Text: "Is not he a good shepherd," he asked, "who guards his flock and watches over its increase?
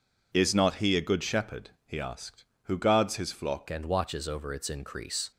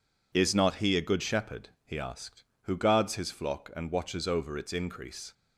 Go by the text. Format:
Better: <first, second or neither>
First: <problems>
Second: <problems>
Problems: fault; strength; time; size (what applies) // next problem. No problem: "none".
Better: second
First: changes voice at "and"; from 3.6 s on; 1.7 s long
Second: none